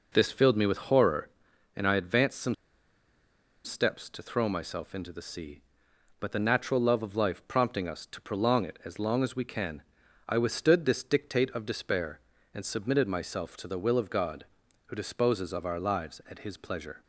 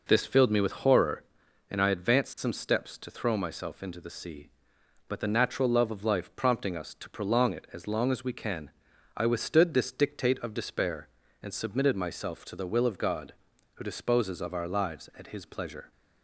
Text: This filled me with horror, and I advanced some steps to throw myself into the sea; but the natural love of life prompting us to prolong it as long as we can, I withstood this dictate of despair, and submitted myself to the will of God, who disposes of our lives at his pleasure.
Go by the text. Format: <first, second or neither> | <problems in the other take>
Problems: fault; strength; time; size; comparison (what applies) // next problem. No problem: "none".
second | pauses between "some" and "steps"; at 2.5 s; 1.1 s long